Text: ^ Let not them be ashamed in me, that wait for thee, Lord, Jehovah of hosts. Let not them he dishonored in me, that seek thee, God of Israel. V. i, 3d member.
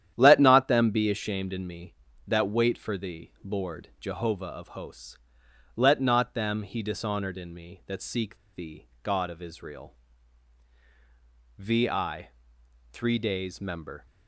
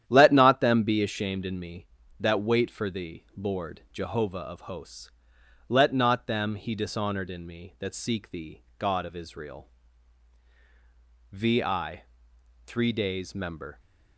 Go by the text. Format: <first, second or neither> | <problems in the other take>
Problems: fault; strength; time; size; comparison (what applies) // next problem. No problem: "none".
second | starts louder than the rest; strong; until 1.1 s; 10.5 dB; strong in the second // pauses between "seek" and "thee"; slight; at 8.3 s; 0.16 s long